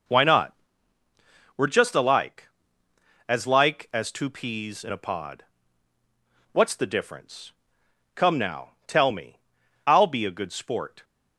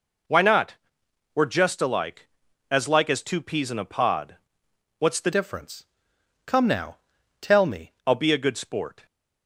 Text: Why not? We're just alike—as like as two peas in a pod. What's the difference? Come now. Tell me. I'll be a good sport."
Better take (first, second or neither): first